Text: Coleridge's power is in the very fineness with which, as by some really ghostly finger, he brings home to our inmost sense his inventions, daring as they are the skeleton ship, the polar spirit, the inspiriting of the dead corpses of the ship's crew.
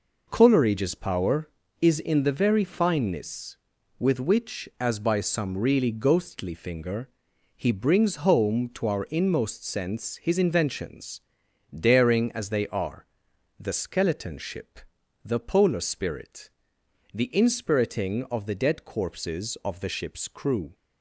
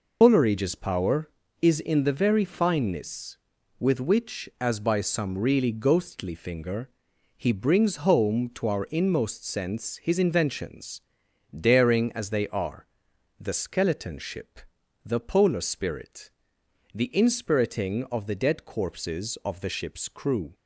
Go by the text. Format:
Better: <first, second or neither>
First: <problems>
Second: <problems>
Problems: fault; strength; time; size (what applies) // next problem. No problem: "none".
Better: first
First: pauses between "are" and "the"; noticeable; at 13.0 s; 0.54 s long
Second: loses the start of "Coleridge's"; at 0.2 s; 110 ms // pauses between "are" and "the"; noticeable; at 12.8 s; 0.54 s long